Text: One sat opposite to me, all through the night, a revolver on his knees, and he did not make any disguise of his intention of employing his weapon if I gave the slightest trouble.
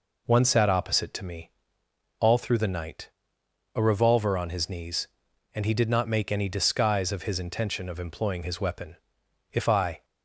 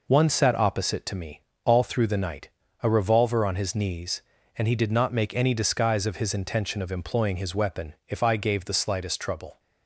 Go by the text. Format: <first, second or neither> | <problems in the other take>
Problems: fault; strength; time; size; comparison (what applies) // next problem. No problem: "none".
second | pauses between "weapon" and "if"; noticeable; at 8.9 s; 0.56 s long // stops before "gave the slightest trouble"; at 10.0 s